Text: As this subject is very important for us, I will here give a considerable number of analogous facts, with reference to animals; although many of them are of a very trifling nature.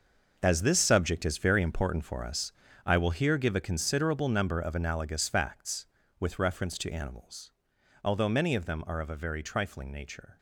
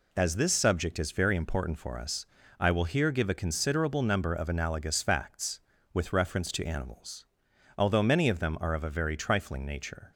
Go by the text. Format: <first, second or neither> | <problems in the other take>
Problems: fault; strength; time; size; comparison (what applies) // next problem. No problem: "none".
second | gets quieter; strong; throughout; 12 dB